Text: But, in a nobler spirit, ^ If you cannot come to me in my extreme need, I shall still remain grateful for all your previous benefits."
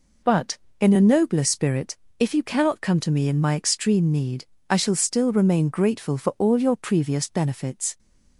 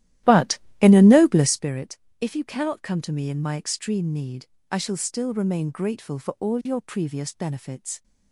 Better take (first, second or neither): first